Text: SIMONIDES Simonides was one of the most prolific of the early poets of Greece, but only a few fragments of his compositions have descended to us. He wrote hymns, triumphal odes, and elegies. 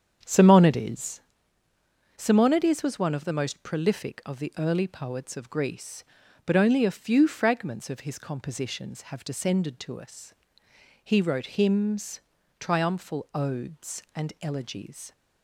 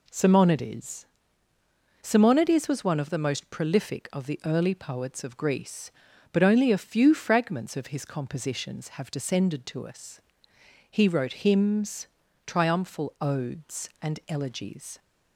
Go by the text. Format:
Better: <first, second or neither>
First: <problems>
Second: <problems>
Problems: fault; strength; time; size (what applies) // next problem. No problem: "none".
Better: second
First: starts louder than the rest; strong; until 1.4 s; 8 dB // pauses between "SIMONIDES" and "Simonides"; noticeable; at 1.1 s; 0.96 s long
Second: pauses between "SIMONIDES" and "Simonides"; noticeable; at 1.0 s; 0.96 s long